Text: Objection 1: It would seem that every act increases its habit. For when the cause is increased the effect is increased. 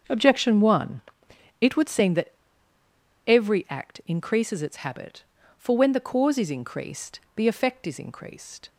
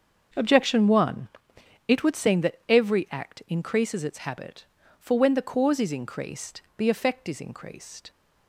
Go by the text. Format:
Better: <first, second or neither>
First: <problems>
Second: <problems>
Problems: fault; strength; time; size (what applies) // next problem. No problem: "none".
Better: second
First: starts louder than the rest; until 1.6 s; 7 dB // pauses between "that" and "every"; noticeable; at 2.3 s; 0.96 s long // pauses between "increased" and "the"; slight; at 7.1 s; 0.16 s long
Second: starts louder than the rest; until 1.9 s; 7 dB // pauses between "increased" and "the"; slight; at 6.6 s; 0.16 s long